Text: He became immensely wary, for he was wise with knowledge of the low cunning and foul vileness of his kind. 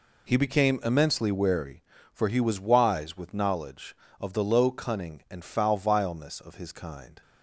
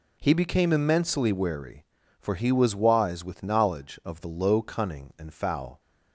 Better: first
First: none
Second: stops before "vileness of his kind"; at 5.8 s

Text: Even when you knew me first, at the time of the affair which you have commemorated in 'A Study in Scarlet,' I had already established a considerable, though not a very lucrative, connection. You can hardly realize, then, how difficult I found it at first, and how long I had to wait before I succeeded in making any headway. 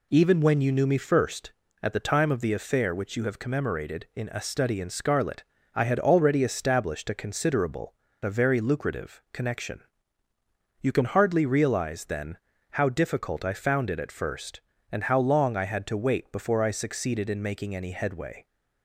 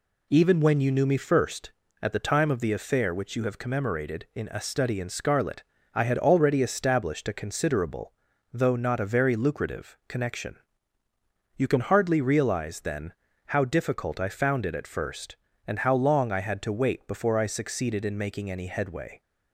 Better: second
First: skips "though not"; at 8.0 s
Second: none

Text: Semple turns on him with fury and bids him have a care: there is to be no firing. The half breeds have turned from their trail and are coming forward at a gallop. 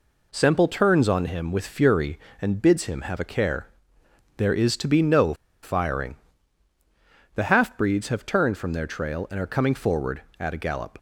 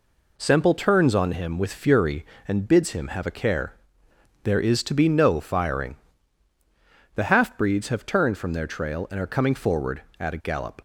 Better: second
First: pauses between "no" and "firing"; slight; at 5.3 s; 0.29 s long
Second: none

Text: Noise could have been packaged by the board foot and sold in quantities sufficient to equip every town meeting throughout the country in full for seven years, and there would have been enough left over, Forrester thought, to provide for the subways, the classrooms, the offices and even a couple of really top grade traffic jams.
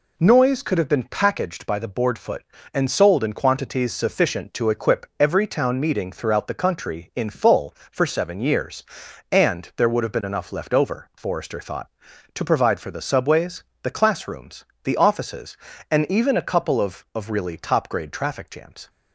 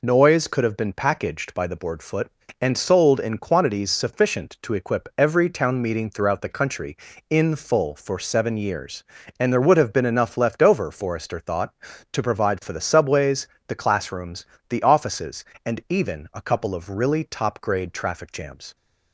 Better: second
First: says "of" twice; at 17.1 s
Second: none

